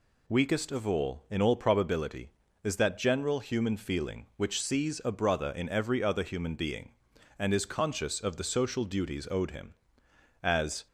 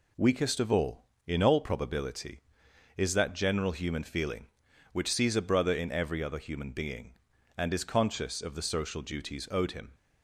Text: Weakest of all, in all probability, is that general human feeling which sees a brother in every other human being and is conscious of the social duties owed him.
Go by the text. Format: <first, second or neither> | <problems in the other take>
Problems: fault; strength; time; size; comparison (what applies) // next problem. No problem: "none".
second | goes on to say "As"; slight; from 10.4 s on; 0.44 s long